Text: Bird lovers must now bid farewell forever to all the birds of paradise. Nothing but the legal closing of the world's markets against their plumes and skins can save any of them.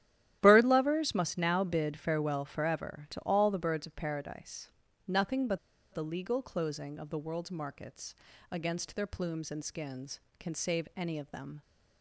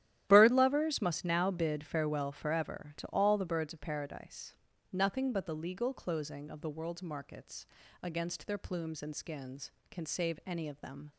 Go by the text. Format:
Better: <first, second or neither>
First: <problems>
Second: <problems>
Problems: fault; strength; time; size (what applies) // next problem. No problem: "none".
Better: second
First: starts louder than the rest; strong; until 1.4 s; 12.5 dB // pauses between "but" and "the"; slight; at 5.5 s; 0.34 s long // pauses between "markets" and "against"; slight; at 8.1 s; 0.36 s long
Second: starts louder than the rest; strong; until 1.2 s; 12.5 dB // pauses between "markets" and "against"; slight; at 7.6 s; 0.36 s long